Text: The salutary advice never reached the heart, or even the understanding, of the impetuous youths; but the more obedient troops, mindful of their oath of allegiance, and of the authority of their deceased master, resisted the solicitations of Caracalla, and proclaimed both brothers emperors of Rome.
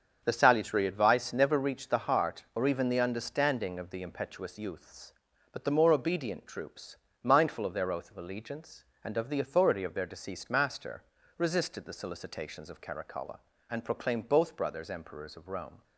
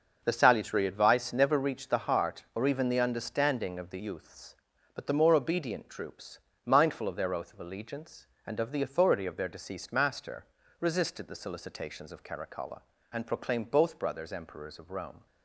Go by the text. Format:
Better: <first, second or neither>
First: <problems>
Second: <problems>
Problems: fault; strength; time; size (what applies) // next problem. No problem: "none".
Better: first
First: starts louder than the rest; strong; until 1.2 s; 7 dB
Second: starts louder than the rest; until 1.2 s; 6.5 dB // skips "impetuous"; at 3.9 s